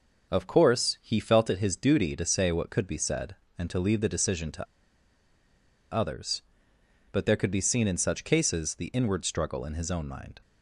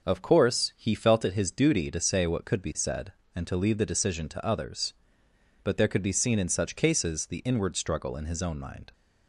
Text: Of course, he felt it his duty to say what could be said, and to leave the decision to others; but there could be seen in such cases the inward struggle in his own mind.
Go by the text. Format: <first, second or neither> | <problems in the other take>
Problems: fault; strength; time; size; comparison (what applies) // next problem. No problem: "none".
second | pauses between "to" and "others"; strong; at 4.6 s; 1.2 s long